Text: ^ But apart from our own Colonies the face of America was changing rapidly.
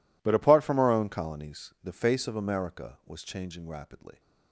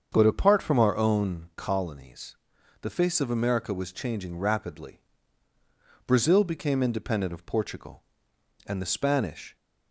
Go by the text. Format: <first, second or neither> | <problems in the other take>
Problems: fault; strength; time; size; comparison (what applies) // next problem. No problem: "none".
first | starts louder than the rest; strong; until 1.1 s; 7 dB // pauses between "Colonies" and "the"; noticeable; at 2.3 s; 0.46 s long // goes on to say "Brazil became independent of Portugal and the Spanish"; strong; from 6.0 s on; 3.5 s long